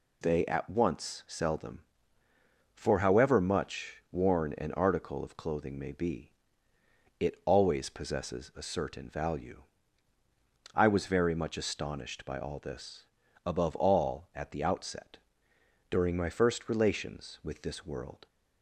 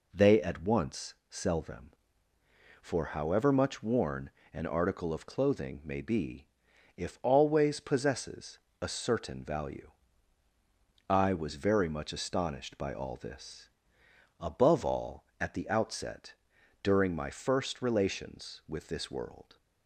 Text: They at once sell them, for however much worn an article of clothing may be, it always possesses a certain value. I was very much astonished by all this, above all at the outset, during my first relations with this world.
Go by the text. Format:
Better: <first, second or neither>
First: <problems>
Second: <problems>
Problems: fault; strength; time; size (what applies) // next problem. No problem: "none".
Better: first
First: none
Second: pauses between "worn" and "an"; slight; at 4.3 s; 0.22 s long // says "if" for "it"; at 6.9 s // pauses between "possesses" and "a"; slight; at 8.5 s; 0.22 s long